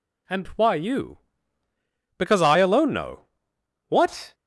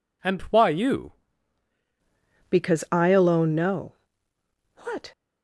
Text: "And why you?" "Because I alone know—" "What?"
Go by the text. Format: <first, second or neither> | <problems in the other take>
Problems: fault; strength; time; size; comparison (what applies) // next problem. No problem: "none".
first | changes voice at "Because"; from 2.4 s on; 2.7 s long